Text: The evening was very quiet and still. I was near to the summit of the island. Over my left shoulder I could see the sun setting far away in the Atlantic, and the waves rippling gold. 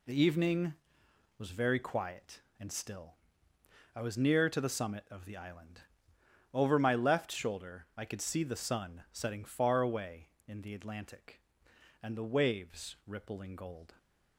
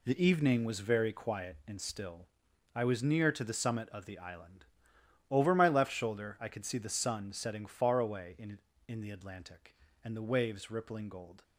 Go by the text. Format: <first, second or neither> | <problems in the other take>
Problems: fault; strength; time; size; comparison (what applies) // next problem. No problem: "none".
first | says "in" twice; at 8.8 s